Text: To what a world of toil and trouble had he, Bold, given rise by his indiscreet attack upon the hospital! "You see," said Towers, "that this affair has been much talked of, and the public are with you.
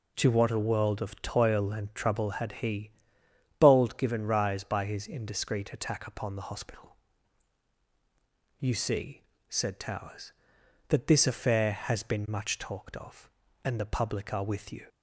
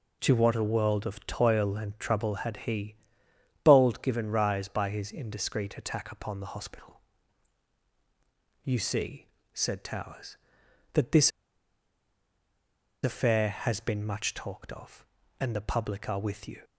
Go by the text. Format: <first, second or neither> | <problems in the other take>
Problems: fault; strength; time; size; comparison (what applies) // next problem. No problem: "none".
first | pauses between "this" and "affair"; strong; at 11.3 s; 1.7 s long